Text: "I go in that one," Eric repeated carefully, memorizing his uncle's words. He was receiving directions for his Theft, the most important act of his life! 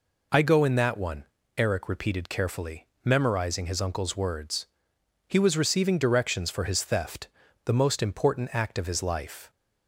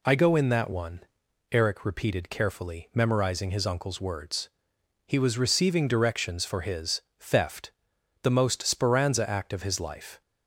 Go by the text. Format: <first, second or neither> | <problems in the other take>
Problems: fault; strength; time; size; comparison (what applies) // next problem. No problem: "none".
first | pauses between "his" and "Theft"; slight; at 7.0 s; 0.18 s long // says "speranza" for "important"; at 8.6 s